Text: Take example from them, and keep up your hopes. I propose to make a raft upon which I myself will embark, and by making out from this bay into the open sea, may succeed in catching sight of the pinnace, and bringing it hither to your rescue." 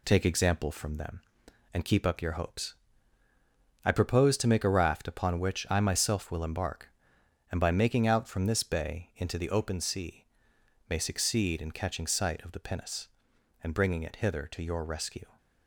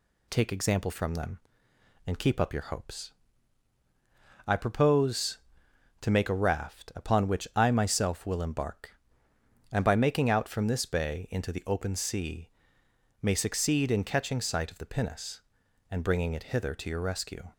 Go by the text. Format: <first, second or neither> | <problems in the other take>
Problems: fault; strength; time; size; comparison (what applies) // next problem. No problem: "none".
second | gets quieter; throughout; 4 dB